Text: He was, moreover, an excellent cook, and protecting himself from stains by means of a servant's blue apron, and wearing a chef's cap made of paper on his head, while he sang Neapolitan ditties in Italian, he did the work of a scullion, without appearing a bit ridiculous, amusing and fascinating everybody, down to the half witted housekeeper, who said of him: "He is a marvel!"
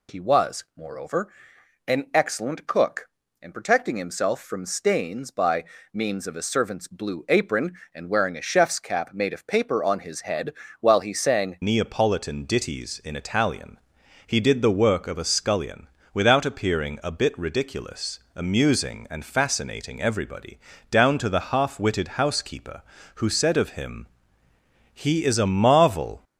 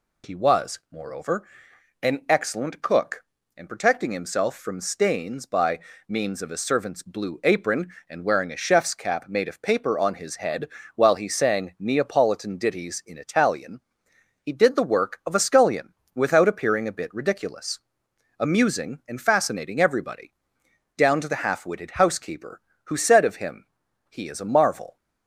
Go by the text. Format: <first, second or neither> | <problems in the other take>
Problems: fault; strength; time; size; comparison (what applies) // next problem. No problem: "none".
second | pauses between "by" and "means"; slight; at 5.6 s; 0.30 s long; slight in the second // changes voice at "Neapolitan"; from 11.6 s on; 14.6 s long